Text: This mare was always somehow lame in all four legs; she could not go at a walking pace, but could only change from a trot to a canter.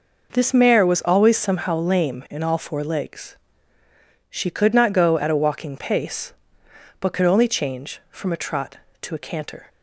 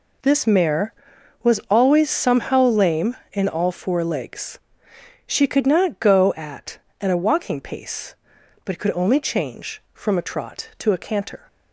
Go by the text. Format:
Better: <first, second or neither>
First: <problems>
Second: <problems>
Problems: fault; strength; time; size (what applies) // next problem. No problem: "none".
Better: first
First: none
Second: says "at" twice; at 6.9 s